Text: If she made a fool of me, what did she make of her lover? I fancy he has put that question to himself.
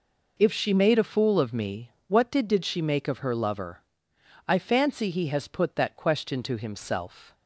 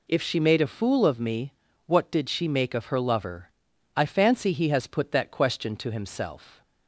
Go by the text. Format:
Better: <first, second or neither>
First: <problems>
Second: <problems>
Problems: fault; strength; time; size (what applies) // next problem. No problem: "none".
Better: second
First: says "did" twice; at 2.4 s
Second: none